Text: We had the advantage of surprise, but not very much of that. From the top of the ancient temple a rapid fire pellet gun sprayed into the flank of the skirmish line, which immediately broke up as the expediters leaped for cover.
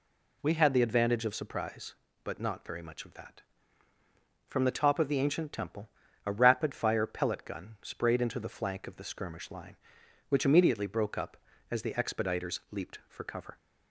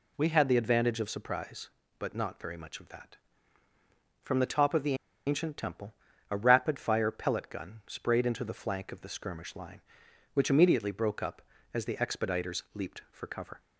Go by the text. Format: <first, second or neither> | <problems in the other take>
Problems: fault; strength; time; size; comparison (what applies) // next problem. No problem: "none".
first | pauses between "the" and "ancient"; slight; at 4.9 s; 0.32 s long // pauses between "temple" and "a"; slight; at 5.9 s; 0.36 s long; slight in the first